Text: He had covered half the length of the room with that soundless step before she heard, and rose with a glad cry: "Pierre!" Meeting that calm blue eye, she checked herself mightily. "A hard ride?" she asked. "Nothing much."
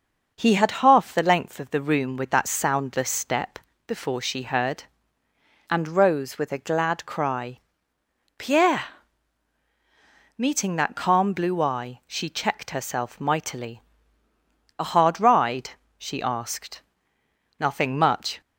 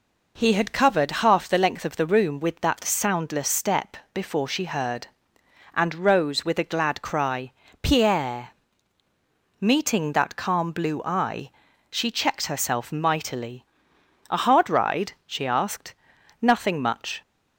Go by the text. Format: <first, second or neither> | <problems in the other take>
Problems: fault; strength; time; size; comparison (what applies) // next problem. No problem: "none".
second | skips "covered"; at 0.8 s // pauses between "step" and "before"; slight; at 3.5 s; 0.28 s long; slight in the second